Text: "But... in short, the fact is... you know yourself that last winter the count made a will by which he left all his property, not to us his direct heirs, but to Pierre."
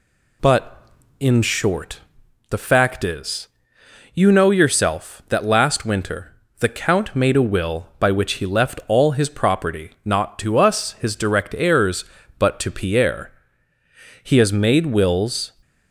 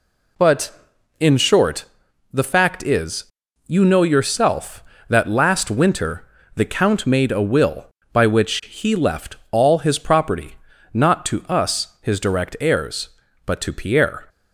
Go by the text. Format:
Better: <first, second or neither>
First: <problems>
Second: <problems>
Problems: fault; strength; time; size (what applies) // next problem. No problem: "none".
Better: second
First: pauses between "winter" and "the"; slight; at 6.3 s; 0.26 s long // goes on to say "He has made wills"; noticeable; from 14.2 s on; 1.2 s long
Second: pauses between "winter" and "the"; slight; at 6.2 s; 0.30 s long